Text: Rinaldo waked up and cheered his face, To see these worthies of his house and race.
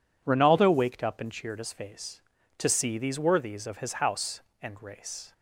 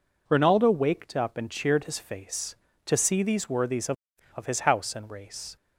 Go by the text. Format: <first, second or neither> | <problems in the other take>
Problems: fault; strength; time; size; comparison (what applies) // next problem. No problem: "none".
first | says "of" twice; at 4.3 s